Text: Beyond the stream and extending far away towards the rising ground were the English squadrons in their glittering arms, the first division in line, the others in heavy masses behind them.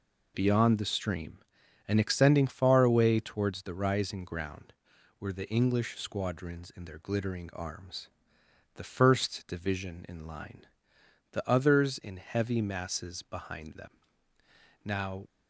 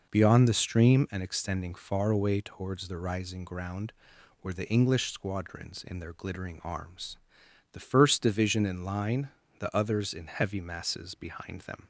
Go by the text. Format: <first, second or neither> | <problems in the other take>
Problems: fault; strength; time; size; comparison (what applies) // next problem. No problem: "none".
second | goes on to say "Now"; slight; from 14.8 s on; 0.44 s long